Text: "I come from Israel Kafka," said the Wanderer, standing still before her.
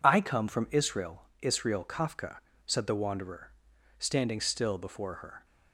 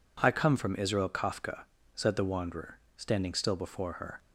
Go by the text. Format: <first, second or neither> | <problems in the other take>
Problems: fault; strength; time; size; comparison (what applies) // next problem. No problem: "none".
second | says "Israel" twice; at 1.4 s